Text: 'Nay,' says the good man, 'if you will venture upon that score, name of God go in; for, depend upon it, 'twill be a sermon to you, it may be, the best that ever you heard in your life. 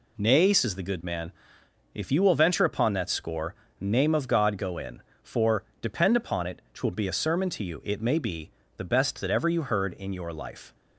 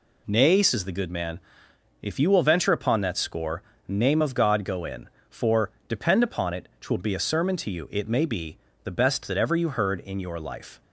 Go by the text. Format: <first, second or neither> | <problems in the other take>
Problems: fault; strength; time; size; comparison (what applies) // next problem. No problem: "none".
neither | none